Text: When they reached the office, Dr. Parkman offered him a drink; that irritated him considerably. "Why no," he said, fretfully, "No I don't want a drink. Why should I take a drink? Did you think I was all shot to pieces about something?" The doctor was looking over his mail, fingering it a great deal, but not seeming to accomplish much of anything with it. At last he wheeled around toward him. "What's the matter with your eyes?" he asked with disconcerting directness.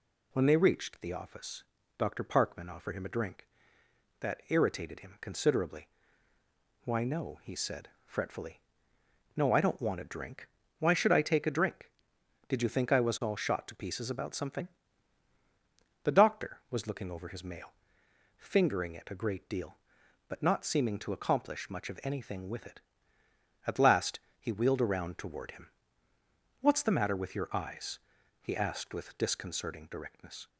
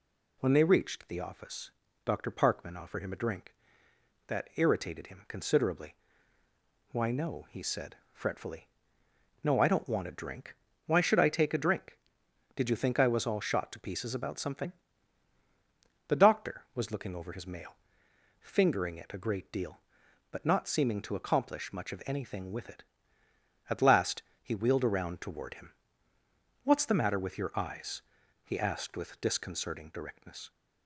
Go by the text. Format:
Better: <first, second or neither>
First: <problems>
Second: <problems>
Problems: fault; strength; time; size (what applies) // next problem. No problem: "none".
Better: neither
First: pauses between "last" and "he"; slight; at 24.1 s; 0.22 s long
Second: pauses between "last" and "he"; slight; at 24.2 s; 0.22 s long